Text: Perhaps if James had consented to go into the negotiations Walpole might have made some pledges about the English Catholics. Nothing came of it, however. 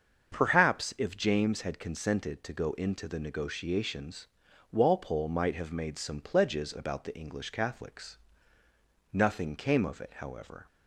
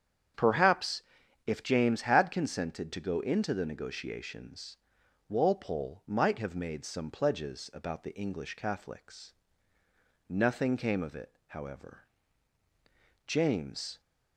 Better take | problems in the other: first | starts louder than the rest; strong; until 1.8 s; 8.5 dB; also in the first // pauses between "Perhaps" and "if"; at 1.0 s; 0.44 s long // pauses between "negotiations" and "Walpole"; noticeable; at 4.7 s; 0.52 s long; noticeable in the first // goes on to say "James"; noticeable; from 13.2 s on; 0.72 s long

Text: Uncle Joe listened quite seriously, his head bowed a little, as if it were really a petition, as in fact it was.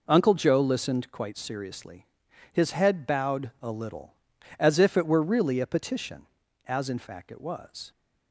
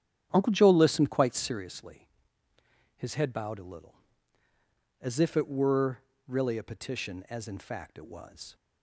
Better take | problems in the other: first | starts louder than the rest; strong; until 1.8 s; 9.5 dB // pauses between "were" and "really"; slight; at 5.9 s; 0.28 s long

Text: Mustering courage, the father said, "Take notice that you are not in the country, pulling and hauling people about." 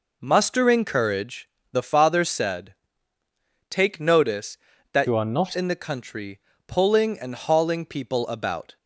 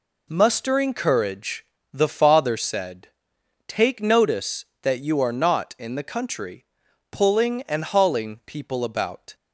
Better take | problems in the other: second | changes voice from "you" to "not"; from 5.0 to 5.5 s; 0.5 s long

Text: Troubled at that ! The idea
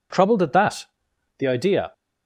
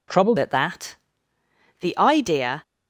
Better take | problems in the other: first | changes voice at "at"; from 0.3 s on; 2.3 s long

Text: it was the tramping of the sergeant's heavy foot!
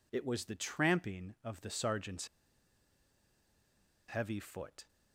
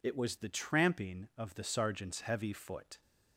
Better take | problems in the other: second | pauses between "sergeant's" and "heavy"; strong; at 2.2 s; 1.8 s long

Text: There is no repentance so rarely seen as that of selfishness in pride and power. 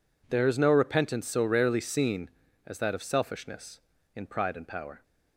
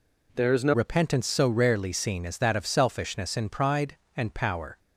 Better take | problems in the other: first | changes voice at "repentance"; from 0.7 s on; 4.0 s long

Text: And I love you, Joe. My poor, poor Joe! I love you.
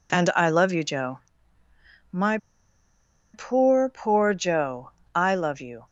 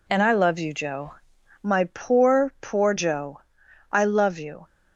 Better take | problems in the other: second | pauses between "My" and "poor"; noticeable; at 2.3 s; 0.96 s long

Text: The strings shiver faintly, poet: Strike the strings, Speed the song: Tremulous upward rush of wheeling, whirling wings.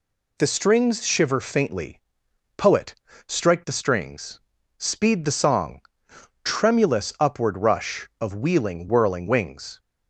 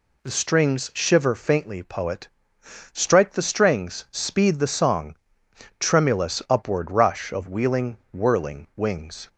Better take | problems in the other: neither | none

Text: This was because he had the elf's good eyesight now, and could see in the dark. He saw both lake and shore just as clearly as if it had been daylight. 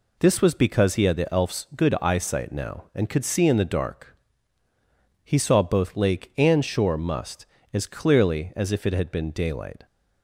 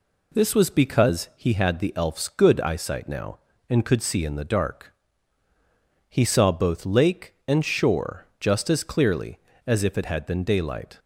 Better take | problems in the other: second | says "must" for "just"; at 6.9 s

